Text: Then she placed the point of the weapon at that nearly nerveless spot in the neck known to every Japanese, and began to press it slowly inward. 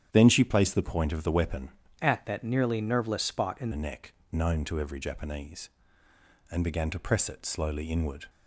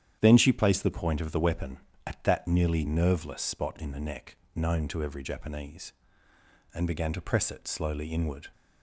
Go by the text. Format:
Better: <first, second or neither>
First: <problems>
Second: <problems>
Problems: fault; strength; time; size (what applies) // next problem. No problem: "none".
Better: second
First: starts louder than the rest; strong; until 1.1 s; 9.5 dB // changes voice from "at" to "in"; from 2.0 to 3.7 s; 1.7 s long // pauses between "neck" and "known"; slight; at 4.1 s; 0.18 s long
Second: starts louder than the rest; strong; until 1.2 s; 9.5 dB // pauses between "neck" and "known"; slight; at 4.3 s; 0.18 s long